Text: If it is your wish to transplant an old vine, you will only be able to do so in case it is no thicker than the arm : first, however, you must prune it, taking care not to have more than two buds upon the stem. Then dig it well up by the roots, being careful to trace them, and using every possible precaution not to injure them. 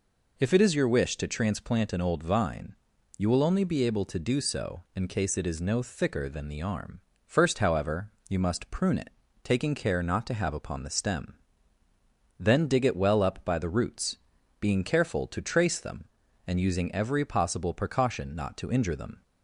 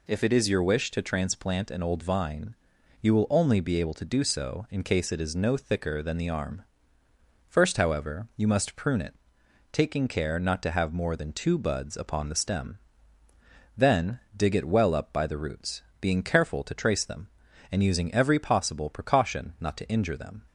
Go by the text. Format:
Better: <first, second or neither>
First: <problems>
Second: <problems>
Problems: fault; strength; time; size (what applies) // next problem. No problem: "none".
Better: second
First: skips "more than two buds"; at 10.5 s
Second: none